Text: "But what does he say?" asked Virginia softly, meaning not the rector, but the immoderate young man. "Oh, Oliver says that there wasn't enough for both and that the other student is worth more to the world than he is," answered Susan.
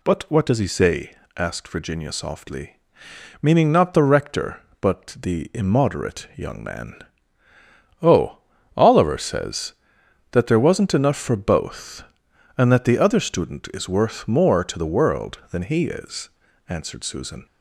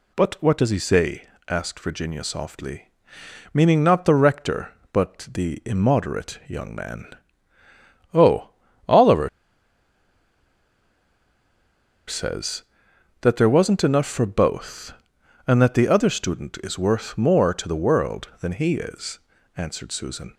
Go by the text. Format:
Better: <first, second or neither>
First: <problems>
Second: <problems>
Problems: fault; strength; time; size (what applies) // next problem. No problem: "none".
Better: first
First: none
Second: pauses between "Oliver" and "says"; strong; at 9.2 s; 2.7 s long